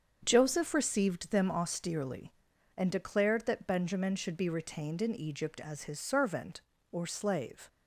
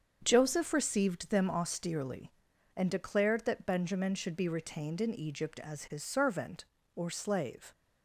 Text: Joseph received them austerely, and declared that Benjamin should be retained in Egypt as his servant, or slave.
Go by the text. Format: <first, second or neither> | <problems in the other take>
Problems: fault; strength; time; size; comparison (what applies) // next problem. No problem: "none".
neither | starts louder than the rest; the same in both